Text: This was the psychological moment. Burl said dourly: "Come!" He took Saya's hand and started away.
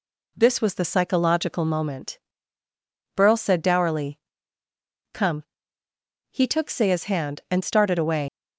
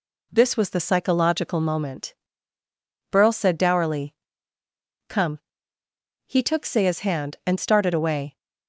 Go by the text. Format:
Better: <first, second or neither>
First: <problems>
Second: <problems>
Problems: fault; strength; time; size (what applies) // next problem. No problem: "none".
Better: second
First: leaves "away" unfinished; at 8.2 s; 130 ms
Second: none